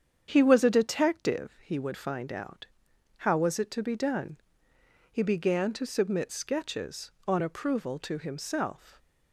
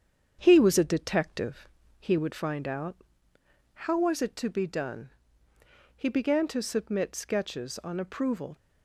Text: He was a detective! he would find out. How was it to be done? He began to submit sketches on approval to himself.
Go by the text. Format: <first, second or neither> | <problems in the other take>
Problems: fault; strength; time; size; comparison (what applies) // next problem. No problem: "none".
first | starts louder than the rest; strong; until 1.4 s; 7.5 dB; strong in the first // stops before "to himself"; at 8.5 s